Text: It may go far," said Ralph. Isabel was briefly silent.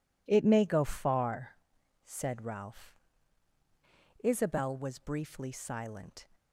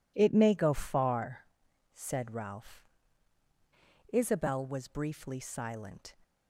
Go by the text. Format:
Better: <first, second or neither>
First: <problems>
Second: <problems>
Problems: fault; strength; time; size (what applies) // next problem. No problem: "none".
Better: neither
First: none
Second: none